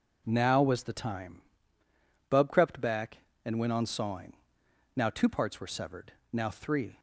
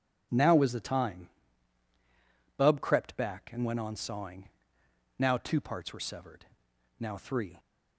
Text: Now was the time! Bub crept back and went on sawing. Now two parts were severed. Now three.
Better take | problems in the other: neither | none

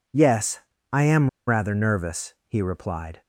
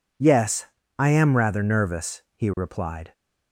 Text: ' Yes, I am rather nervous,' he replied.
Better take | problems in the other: second | pauses between "am" and "rather"; slight; at 1.2 s; 0.18 s long

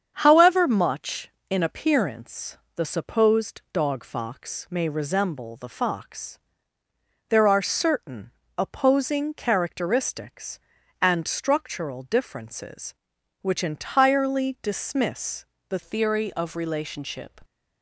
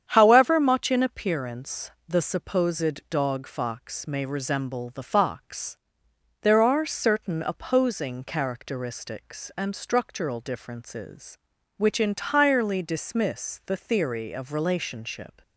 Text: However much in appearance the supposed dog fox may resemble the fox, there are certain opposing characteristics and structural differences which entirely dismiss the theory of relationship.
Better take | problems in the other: second | starts louder than the rest; strong; until 1.1 s; 7.5 dB; strong in the second // pauses between "appearance" and "the"; slight; at 2.5 s; 0.20 s long; slight in the second // pauses between "certain" and "opposing"; slight; at 8.3 s; 0.26 s long // pauses between "dismiss" and "the"; slight; at 15.4 s; 0.24 s long // changes voice at "theory"; from 15.8 s on; 1.5 s long

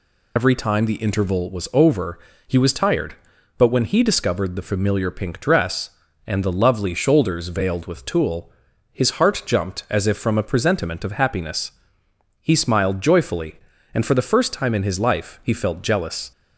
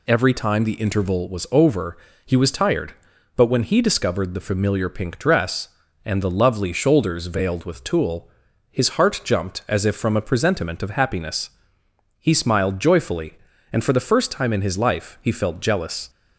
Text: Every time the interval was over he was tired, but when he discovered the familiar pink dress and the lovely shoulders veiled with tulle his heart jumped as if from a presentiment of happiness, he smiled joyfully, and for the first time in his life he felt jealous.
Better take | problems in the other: second | loses the start of "Every"; at 0.3 s; 65 ms // pauses between "over" and "he"; slight; at 2.1 s; 0.30 s long; slight in the second // pauses between "tulle" and "his"; at 8.5 s; 0.40 s long; also in the second

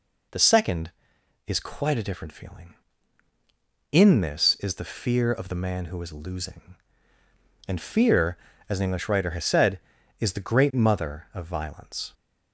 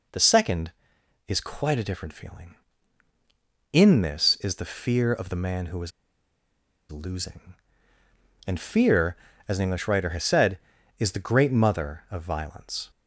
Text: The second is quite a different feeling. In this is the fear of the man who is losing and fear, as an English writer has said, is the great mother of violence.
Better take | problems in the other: first | pauses between "is" and "losing"; at 5.9 s; 0.99 s long

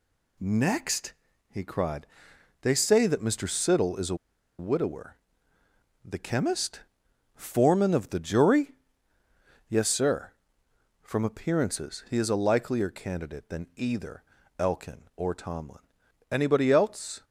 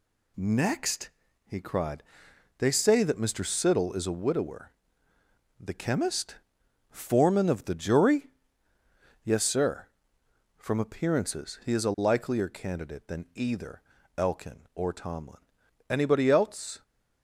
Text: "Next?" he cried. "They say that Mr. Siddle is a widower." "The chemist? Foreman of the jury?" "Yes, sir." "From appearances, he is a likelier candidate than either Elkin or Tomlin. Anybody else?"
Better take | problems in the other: second | pauses between "a" and "widower"; at 4.1 s; 0.44 s long // pauses between "either" and "Elkin"; slight; at 14.2 s; 0.34 s long; slight in the second

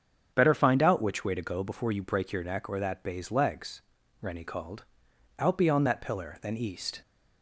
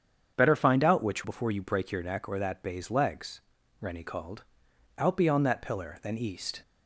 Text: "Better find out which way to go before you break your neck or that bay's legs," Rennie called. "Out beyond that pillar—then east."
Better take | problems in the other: first | starts louder than the rest; strong; until 1.3 s; 7.5 dB; also in the first // skips "way to go"; at 1.2 s

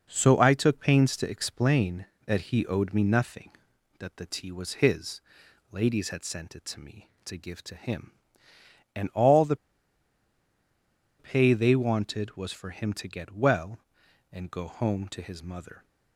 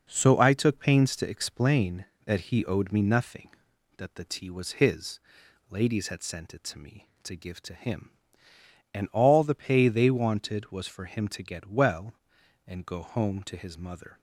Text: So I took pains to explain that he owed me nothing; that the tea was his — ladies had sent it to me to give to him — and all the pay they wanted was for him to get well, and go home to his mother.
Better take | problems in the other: second | pauses between "the" and "pay"; strong; at 9.5 s; 1.6 s long

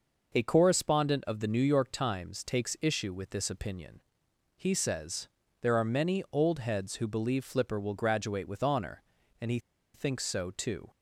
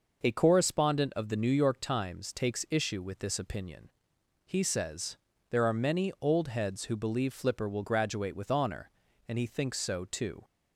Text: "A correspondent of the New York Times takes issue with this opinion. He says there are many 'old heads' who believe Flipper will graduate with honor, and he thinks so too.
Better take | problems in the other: second | pauses between "says" and "there"; slight; at 5.2 s; 0.32 s long; slight in the second // pauses between "he" and "thinks"; slight; at 9.5 s; 0.35 s long

